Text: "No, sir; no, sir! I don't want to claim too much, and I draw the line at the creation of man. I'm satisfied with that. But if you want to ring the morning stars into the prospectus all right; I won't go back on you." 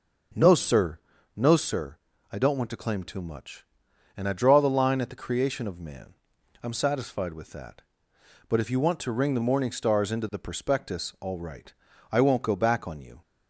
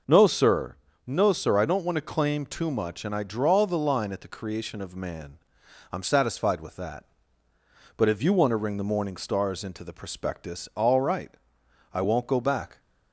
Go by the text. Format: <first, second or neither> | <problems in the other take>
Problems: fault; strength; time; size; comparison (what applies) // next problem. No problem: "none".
first | stops before "on you"; at 12.7 s